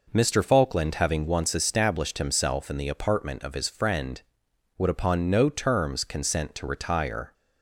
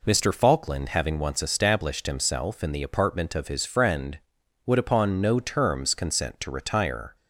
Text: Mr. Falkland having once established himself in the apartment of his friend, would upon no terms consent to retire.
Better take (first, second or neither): neither